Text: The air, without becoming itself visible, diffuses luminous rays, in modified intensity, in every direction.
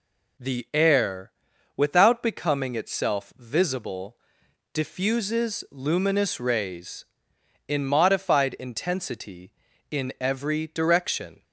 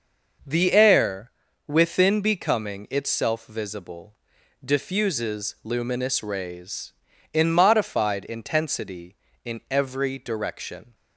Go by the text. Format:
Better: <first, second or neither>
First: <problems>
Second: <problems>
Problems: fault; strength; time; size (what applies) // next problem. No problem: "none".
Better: first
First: none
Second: starts louder than the rest; noticeable; until 1.8 s; 6 dB // says "within" for "without"; at 1.6 s